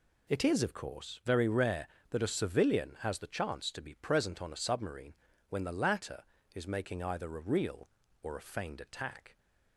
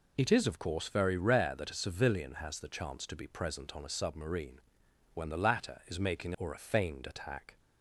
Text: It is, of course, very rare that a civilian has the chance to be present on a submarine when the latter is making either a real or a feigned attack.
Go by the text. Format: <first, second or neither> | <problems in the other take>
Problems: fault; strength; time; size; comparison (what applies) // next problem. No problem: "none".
first | pauses between "submarine" and "when"; noticeable; at 4.5 s; 0.54 s long; slight in the first // skips "either a real"; at 6.3 s